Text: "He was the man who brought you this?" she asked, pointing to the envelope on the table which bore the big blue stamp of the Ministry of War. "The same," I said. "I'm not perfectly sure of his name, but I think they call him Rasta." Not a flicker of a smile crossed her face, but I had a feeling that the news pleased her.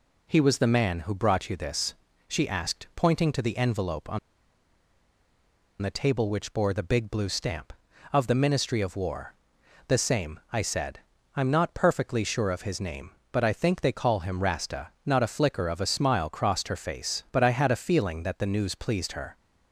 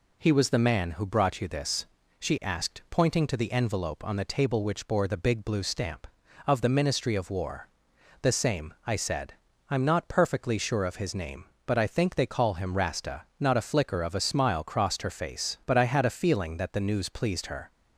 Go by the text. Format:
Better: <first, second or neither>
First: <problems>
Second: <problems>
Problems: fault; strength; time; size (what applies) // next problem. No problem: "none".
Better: second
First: pauses between "on" and "the"; strong; at 4.1 s; 1.6 s long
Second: none